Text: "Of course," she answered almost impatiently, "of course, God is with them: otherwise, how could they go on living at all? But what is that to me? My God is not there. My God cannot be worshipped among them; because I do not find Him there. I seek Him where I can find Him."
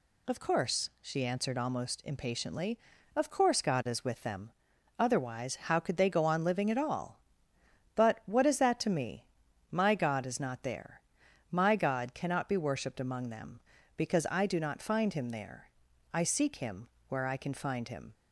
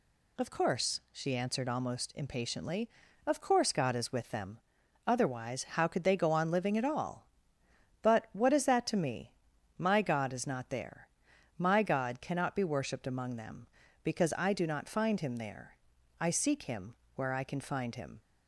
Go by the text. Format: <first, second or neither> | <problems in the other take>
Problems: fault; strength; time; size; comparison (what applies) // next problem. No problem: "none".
neither | pauses between "Him" and "where"; slight; the same in both